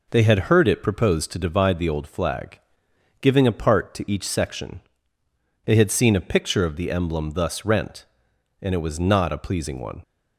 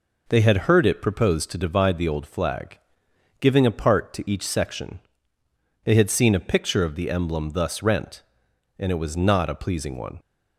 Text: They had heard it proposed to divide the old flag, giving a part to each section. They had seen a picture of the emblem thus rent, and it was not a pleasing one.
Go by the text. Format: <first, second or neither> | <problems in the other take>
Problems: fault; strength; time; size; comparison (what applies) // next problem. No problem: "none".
neither | none